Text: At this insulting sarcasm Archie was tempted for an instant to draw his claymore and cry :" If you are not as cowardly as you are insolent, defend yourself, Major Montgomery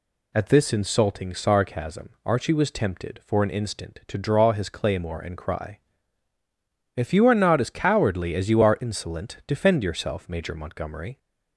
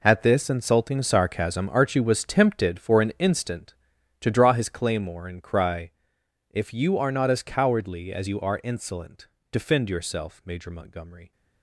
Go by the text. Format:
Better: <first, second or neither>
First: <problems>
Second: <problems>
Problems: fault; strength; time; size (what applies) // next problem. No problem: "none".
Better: first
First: none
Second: gets quieter; strong; throughout; 13.5 dB